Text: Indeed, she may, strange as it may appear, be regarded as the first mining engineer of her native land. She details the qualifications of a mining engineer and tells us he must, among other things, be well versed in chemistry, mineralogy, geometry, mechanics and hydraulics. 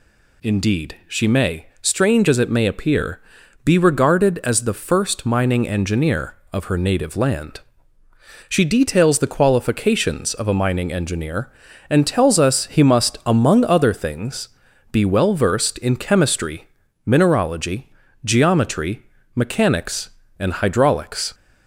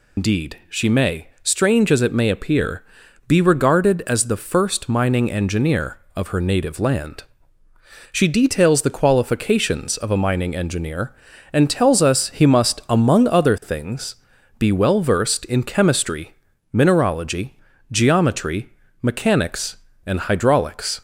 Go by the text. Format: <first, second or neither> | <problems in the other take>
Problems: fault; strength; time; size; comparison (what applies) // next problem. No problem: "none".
first | loses the start of "Indeed"; at 0.1 s; 140 ms